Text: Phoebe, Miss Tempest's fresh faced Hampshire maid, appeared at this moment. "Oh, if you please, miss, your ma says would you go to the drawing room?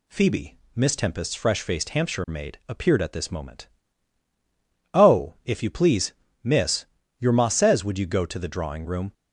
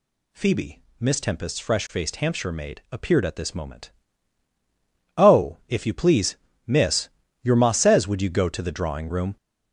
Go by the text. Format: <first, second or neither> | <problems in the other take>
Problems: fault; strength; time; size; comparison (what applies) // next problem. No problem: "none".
first | gets louder; throughout; 7 dB